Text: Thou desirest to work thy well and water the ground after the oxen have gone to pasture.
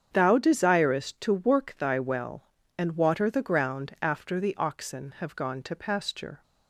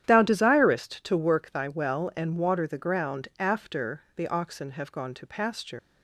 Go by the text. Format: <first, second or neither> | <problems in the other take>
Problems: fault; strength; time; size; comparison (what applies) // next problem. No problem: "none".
first | starts louder than the rest; strong; until 1.0 s; 10.5 dB; strong in the first // leaves "pasture" unfinished; at 5.7 s; 165 ms